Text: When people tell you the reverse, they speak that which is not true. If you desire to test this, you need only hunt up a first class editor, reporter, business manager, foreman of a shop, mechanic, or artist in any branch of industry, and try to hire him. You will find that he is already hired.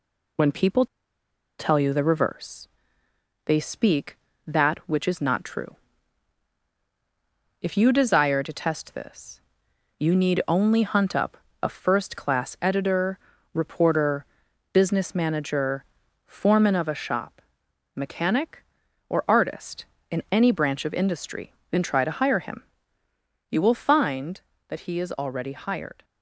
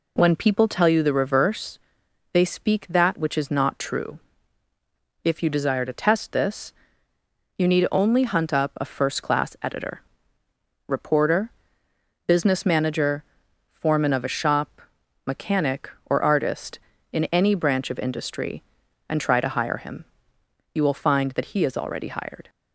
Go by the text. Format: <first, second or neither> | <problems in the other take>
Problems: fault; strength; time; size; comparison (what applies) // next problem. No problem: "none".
second | pauses between "people" and "tell"; noticeable; at 0.8 s; 0.73 s long // pauses between "up" and "a"; slight; at 11.3 s; 0.26 s long